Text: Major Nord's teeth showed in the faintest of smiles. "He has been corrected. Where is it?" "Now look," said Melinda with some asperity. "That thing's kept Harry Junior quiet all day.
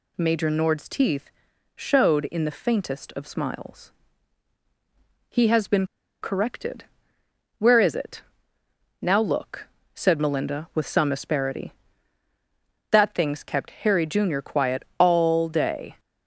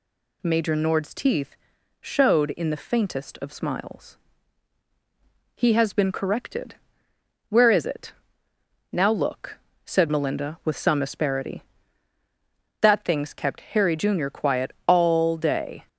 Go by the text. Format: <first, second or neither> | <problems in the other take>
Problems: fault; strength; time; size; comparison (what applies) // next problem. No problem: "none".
second | pauses between "teeth" and "showed"; at 1.3 s; 0.44 s long; also in the second // pauses between "been" and "corrected"; slight; at 5.8 s; 0.35 s long